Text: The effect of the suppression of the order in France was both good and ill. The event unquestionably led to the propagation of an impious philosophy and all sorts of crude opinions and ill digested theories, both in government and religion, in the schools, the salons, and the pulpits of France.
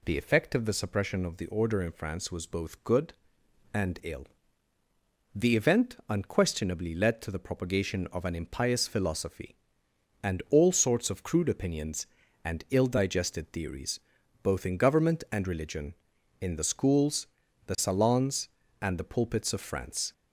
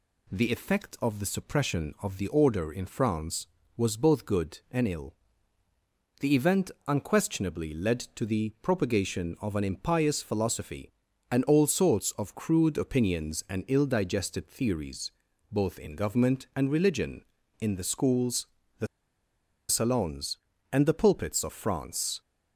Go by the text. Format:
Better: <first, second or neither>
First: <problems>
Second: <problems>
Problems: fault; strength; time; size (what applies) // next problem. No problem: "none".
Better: first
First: none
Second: pauses between "event" and "unquestionably"; slight; at 6.7 s; 0.16 s long // pauses between "the" and "salons"; noticeable; at 18.8 s; 0.83 s long